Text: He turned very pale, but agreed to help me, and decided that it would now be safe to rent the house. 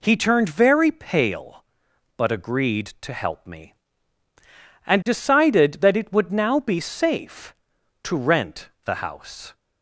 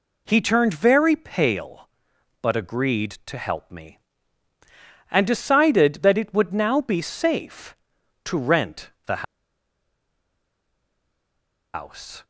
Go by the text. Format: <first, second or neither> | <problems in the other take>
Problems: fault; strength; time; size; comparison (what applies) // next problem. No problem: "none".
first | pauses between "rent" and "the"; slight; at 8.9 s; 0.16 s long; slight in the first // pauses between "the" and "house"; strong; at 9.2 s; 2.5 s long